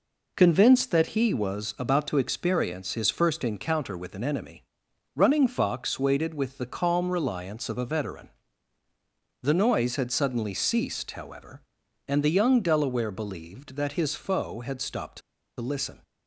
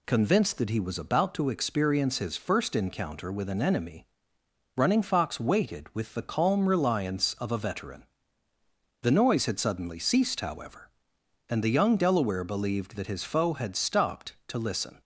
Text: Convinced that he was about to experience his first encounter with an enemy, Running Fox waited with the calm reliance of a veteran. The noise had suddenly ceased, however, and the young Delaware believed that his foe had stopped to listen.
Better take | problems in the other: second | pauses between "to" and "listen"; at 15.2 s; 0.39 s long

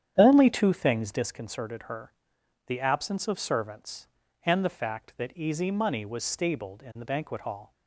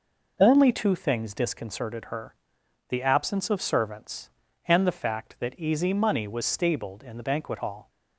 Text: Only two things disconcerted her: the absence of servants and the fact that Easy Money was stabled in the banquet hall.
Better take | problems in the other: second | starts louder than the rest; strong; until 1.2 s; 9 dB

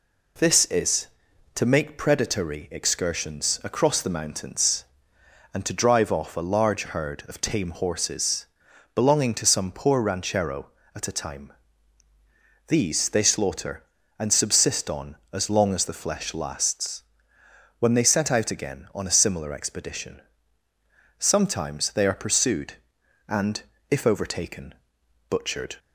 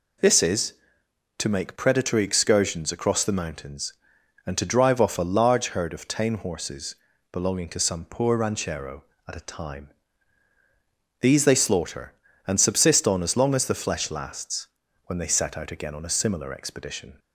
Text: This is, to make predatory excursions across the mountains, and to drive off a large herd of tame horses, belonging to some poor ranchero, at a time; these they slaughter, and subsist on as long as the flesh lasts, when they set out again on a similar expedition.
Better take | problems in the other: second | goes on to say "Sometimes they are pursued and if overtaken butchered"; strong; from 21.1 s on; 4.6 s long

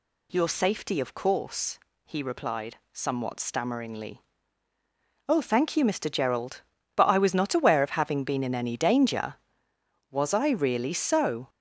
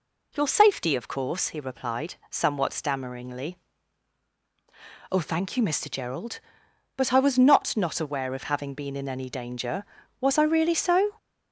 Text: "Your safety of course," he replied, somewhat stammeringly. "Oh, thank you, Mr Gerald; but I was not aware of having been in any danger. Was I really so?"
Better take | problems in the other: first | says "not" twice; at 7.7 s

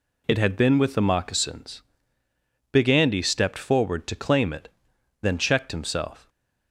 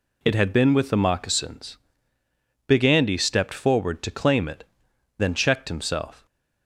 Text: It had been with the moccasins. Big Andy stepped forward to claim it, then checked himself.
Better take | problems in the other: neither | none

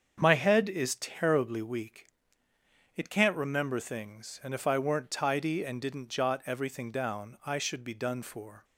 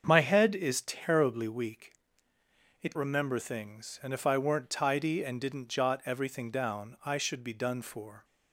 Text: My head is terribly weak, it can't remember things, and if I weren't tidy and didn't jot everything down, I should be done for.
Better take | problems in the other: first | starts louder than the rest; until 1.0 s; 7 dB; also in the first // skips "can't"; at 2.9 s

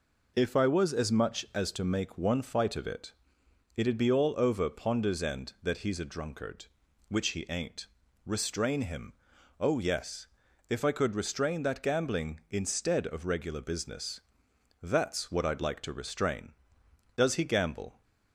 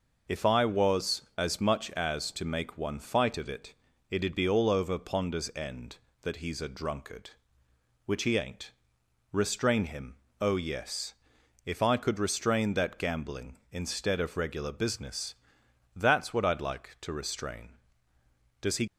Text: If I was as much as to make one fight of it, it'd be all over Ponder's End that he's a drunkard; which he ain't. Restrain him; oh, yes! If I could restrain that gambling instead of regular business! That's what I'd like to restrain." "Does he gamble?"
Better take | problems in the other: first | stops before "gamble"; at 18.8 s

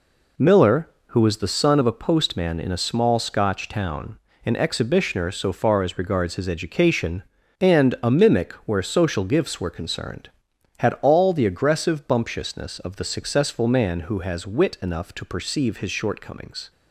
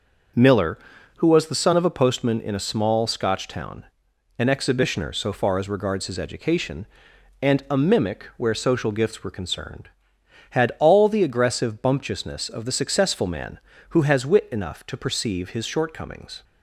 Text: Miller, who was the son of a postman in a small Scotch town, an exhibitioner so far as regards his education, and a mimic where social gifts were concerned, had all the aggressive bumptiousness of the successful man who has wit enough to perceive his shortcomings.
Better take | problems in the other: neither | none

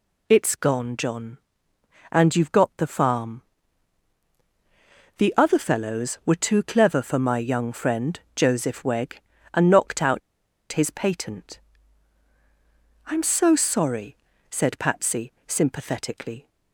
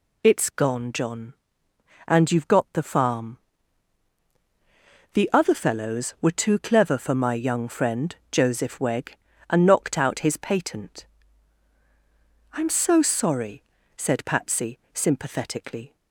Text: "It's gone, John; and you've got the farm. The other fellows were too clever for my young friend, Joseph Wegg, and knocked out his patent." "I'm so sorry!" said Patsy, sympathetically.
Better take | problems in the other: second | pauses between "out" and "his"; noticeable; at 10.2 s; 0.52 s long

